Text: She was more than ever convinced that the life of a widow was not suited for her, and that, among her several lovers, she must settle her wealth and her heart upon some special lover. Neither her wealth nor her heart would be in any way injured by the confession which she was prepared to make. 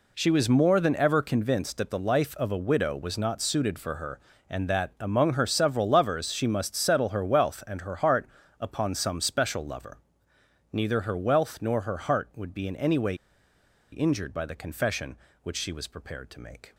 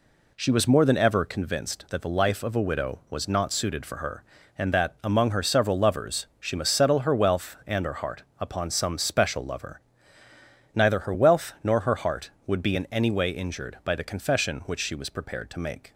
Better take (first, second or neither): second